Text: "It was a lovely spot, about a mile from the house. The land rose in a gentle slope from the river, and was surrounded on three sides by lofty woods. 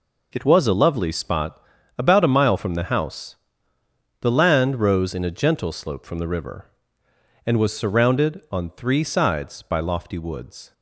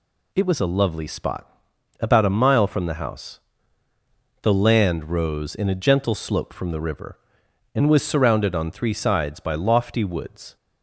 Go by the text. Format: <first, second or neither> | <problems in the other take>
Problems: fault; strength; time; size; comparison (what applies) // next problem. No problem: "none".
neither | none